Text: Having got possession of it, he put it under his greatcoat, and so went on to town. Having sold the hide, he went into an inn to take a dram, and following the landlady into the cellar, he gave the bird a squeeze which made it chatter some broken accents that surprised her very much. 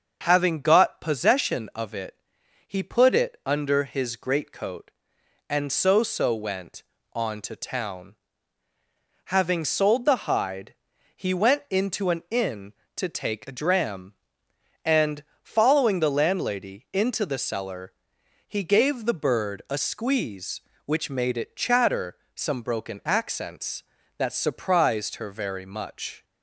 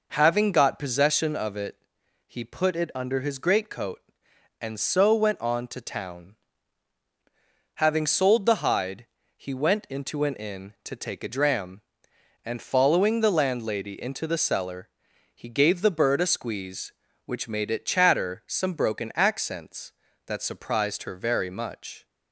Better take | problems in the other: second | starts louder than the rest; until 1.2 s; 6.5 dB // says "so" twice; at 6.0 s // pauses between "and" and "following"; slight; at 15.2 s; 0.18 s long // pauses between "chatter" and "some"; slight; at 22.1 s; 0.22 s long

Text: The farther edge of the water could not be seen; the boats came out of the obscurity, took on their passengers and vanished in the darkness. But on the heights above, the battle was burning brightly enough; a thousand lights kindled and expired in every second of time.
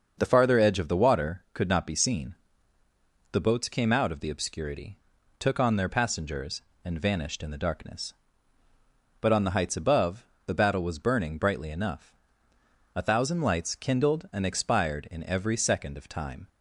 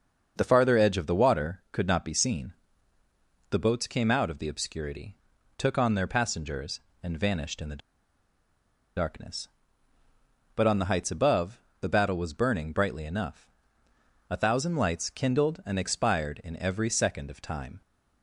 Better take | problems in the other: first | starts louder than the rest; until 1.3 s; 6.5 dB; also in the first // pauses between "the" and "darkness"; at 7.8 s; 1.1 s long

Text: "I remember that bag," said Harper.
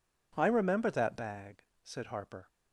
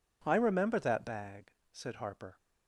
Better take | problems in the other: neither | none

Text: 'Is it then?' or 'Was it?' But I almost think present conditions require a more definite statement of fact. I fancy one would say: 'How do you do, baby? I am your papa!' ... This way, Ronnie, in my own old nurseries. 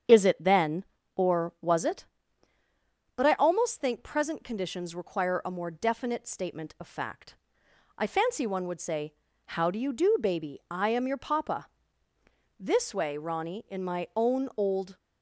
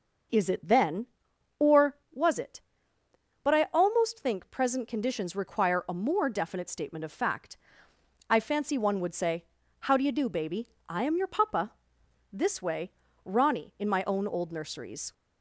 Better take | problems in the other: second | starts louder than the rest; strong; until 1.3 s; 8 dB; noticeable in the second // stops before "nurseries"; at 14.9 s

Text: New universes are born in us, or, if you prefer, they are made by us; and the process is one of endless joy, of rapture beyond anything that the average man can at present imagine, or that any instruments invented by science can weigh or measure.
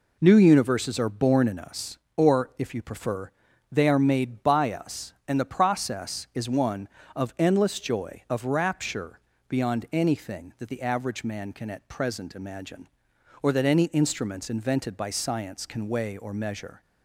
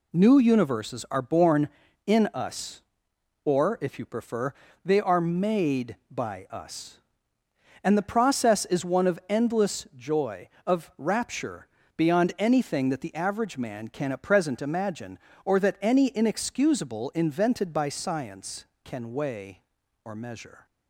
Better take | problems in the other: first | pauses between "rapture" and "beyond"; slight; at 11.6 s; 0.28 s long; slight in the first // says "inexcusable" for "instruments"; at 16.1 s

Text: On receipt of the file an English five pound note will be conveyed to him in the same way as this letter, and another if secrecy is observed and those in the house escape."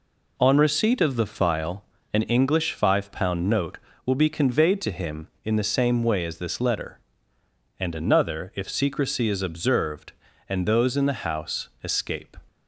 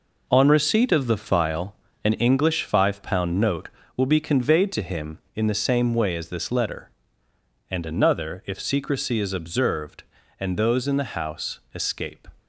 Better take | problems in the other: first | gets quieter; strong; throughout; 7 dB // pauses between "file" and "an"; slight; at 1.7 s; 0.30 s long; slight in the first

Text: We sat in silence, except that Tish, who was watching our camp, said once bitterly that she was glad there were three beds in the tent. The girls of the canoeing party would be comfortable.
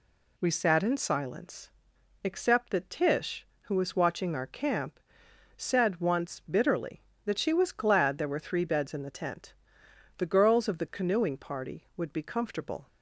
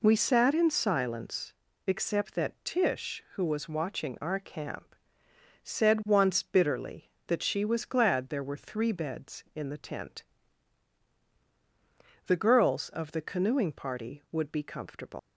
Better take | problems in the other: first | leaves "comfortable" unfinished; at 15.1 s; 110 ms

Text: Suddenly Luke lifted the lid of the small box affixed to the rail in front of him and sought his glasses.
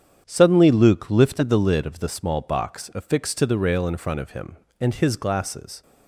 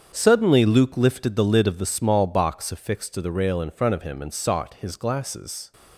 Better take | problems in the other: second | starts louder than the rest; strong; until 1.2 s; 8.5 dB; strong in the second // skips "sought"; at 4.9 s

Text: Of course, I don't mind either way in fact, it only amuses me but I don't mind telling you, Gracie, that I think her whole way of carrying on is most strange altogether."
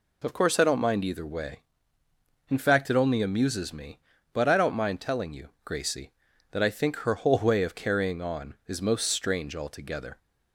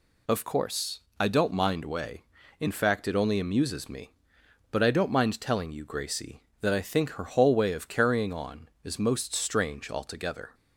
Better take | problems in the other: first | skips "either"; at 1.8 s

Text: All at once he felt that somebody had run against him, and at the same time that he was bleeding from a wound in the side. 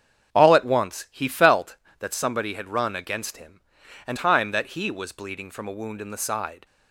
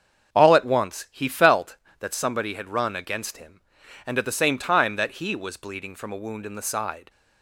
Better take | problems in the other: second | starts louder than the rest; strong; until 1.3 s; 7.5 dB; also in the second // skips "at the same"; at 4.1 s

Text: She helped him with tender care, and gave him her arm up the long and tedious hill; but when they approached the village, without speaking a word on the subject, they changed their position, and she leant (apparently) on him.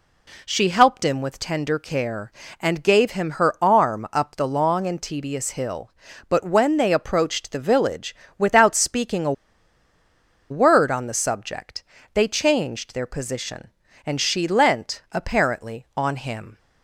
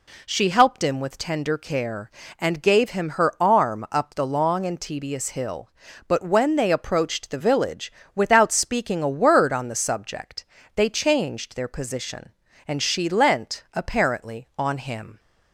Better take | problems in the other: second | pauses between "a" and "word"; at 9.3 s; 1.1 s long

